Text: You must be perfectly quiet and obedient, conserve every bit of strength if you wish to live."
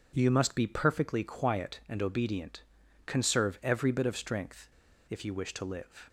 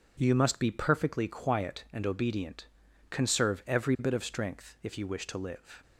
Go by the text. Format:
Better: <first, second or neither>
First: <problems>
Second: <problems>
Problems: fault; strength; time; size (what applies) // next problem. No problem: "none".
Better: second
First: pauses between "strength" and "if"; at 4.6 s; 0.42 s long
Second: none